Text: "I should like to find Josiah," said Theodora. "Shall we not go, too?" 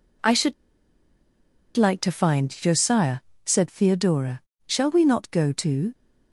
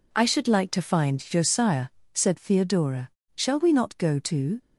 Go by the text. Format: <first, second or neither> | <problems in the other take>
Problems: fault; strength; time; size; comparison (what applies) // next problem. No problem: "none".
second | pauses between "should" and "like"; at 0.5 s; 1.2 s long